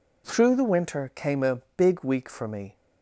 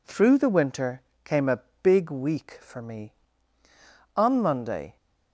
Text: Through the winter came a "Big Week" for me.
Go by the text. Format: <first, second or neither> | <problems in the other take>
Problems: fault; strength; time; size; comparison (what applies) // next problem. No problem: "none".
first | pauses between "winter" and "came"; slight; at 0.9 s; 0.24 s long // pauses between "a" and "Big"; slight; at 1.6 s; 0.20 s long; slight in the first // goes on to say "On Monday"; noticeable; from 4.1 s on; 0.80 s long